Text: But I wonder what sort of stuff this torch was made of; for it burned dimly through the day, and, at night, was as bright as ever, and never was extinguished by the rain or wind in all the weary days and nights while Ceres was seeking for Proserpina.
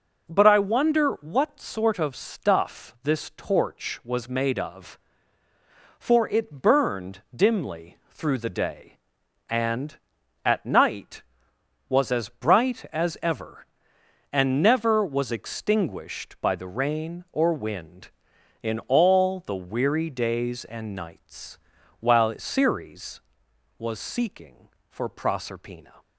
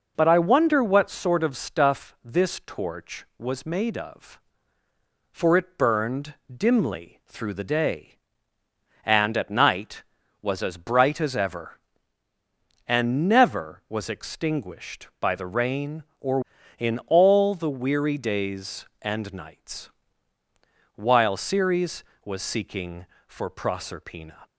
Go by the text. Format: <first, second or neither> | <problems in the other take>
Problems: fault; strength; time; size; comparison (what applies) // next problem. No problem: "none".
first | pauses between "burned" and "dimly"; slight; at 6.3 s; 0.18 s long // skips "wind"; at 16.5 s // pauses between "nights" and "while"; at 19.8 s; 1.0 s long; also in the first